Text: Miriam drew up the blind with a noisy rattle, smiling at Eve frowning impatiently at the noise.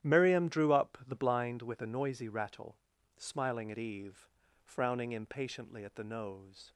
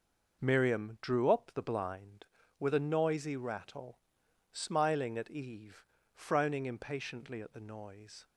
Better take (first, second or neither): second